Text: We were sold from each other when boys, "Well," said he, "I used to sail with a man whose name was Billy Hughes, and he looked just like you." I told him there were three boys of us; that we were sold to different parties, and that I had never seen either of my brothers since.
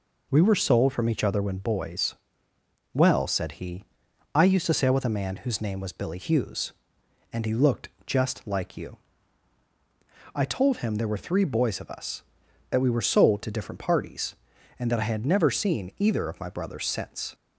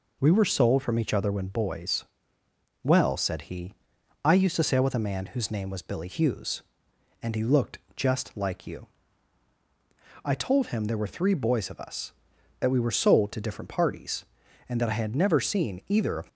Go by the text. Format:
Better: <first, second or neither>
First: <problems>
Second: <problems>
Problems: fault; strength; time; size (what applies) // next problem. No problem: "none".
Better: first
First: pauses between "looked" and "just"; slight; at 7.8 s; 0.16 s long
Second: pauses between "looked" and "just"; slight; at 7.7 s; 0.16 s long // stops before "my brothers since"; at 16.2 s